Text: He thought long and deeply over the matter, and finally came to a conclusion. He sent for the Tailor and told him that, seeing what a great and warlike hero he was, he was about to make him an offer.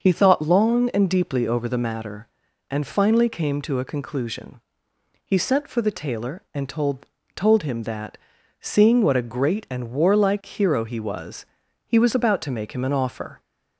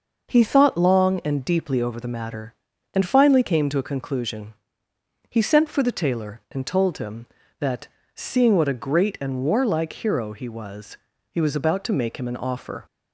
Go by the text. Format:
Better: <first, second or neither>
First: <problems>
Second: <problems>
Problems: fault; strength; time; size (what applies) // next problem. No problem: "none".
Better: second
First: starts louder than the rest; noticeable; until 1.0 s; 6 dB // says "told" twice; at 7.3 s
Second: none